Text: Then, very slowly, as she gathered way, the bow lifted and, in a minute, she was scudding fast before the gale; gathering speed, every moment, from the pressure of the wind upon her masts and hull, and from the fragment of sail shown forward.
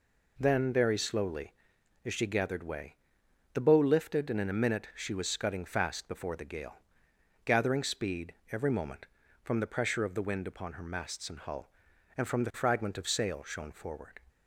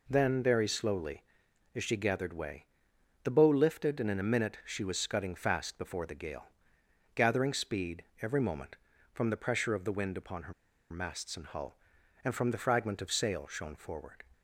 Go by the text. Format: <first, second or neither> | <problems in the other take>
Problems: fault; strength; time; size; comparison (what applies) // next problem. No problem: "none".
first | pauses between "her" and "masts"; at 10.5 s; 0.37 s long